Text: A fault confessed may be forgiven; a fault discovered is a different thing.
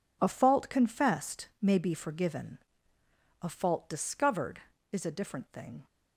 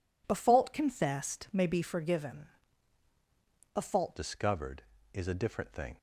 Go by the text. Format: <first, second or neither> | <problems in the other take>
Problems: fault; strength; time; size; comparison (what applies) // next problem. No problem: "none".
first | changes voice at "discovered"; from 4.1 s on; 1.8 s long